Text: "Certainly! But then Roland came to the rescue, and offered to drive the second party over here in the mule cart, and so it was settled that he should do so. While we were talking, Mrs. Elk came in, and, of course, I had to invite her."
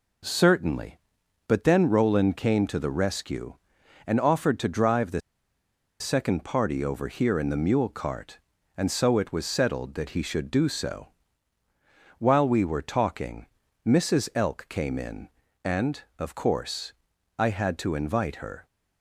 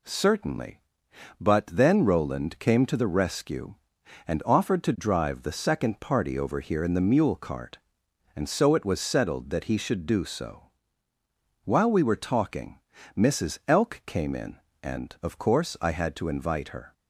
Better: second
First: pauses between "the" and "second"; noticeable; at 5.1 s; 0.80 s long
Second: none

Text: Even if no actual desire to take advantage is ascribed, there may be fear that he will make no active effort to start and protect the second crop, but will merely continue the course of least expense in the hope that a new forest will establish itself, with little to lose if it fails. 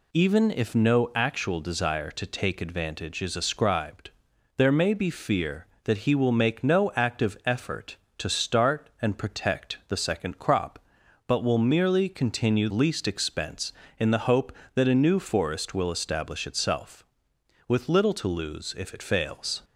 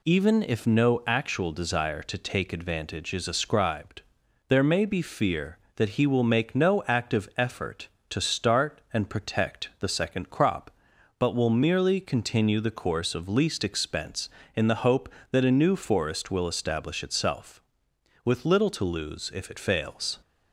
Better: second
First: skips "the course of"; at 12.6 s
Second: none

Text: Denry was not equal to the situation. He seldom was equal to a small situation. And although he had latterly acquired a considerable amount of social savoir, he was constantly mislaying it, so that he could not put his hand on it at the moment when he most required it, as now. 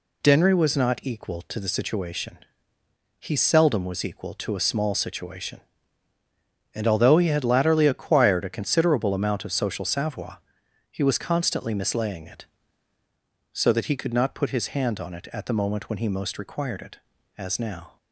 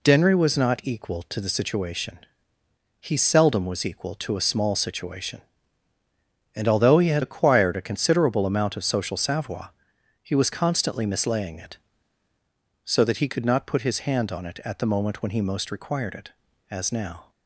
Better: first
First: none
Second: skips "latterly"; at 7.2 s

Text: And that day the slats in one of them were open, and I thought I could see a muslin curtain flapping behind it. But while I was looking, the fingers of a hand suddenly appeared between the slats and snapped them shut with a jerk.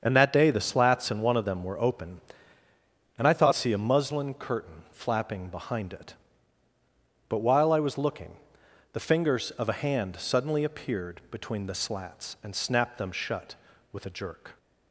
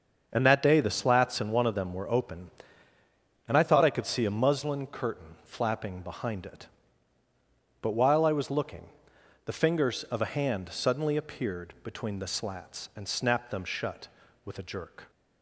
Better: second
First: starts louder than the rest; until 1.0 s; 7 dB // skips "I could"; at 3.5 s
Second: starts louder than the rest; until 1.3 s; 6.5 dB

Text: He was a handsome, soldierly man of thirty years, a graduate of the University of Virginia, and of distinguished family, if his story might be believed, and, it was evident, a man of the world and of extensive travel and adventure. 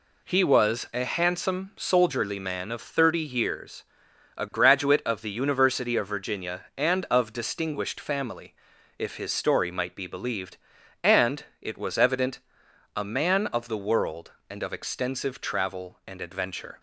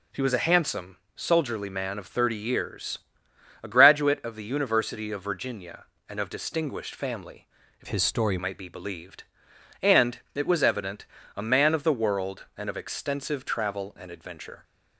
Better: first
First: none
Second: changes voice from "his" to "story"; from 7.8 to 8.3 s; 0.5 s long

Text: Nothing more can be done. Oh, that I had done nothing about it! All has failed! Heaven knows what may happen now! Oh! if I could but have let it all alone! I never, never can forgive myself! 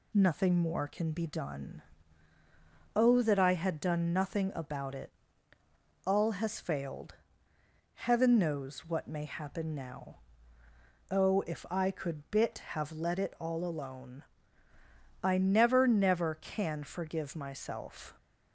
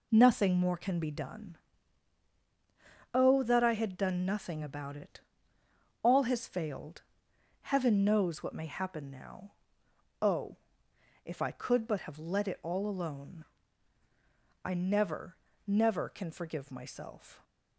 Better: second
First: says "bit" for "but"; at 12.3 s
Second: none

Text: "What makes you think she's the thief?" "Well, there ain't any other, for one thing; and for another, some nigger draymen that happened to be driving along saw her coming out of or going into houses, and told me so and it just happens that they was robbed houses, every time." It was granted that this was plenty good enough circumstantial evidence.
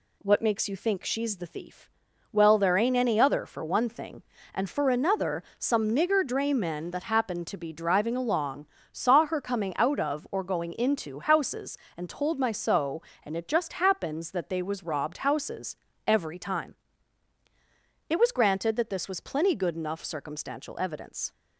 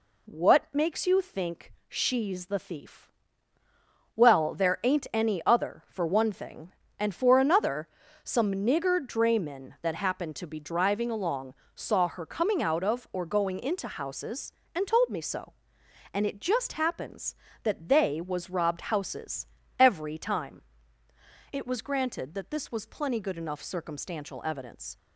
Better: second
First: pauses between "along" and "saw"; slight; at 8.6 s; 0.24 s long // says "my" for "me"; at 12.3 s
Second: pauses between "along" and "saw"; slight; at 11.5 s; 0.22 s long

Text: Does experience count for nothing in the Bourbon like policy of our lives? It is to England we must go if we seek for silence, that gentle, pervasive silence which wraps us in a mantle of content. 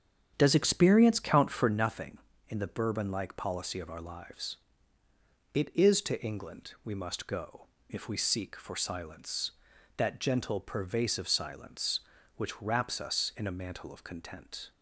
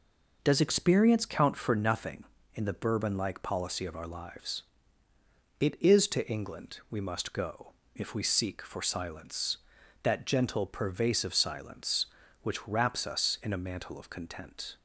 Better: second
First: starts louder than the rest; strong; until 1.9 s; 8 dB // pauses between "go" and "if"; slight; at 7.6 s; 0.22 s long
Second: pauses between "go" and "if"; slight; at 7.7 s; 0.22 s long

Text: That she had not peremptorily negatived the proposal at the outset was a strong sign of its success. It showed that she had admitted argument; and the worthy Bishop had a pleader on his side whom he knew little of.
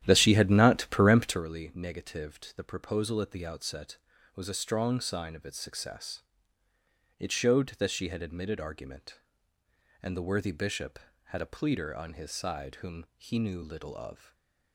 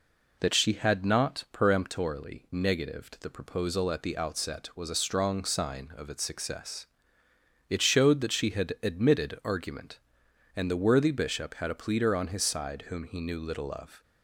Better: second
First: starts louder than the rest; strong; until 1.5 s; 11 dB // stays silent after the last word; slight; from 14.1 s on; 0.6 s long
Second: none

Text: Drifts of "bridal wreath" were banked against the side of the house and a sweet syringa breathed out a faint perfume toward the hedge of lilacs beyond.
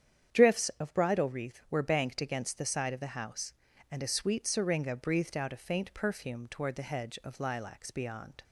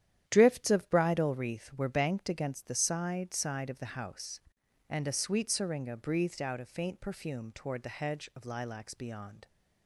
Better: first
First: starts louder than the rest; strong; until 1.4 s; 9 dB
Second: starts louder than the rest; strong; until 1.2 s; 10.5 dB // says "side" twice; at 3.3 s

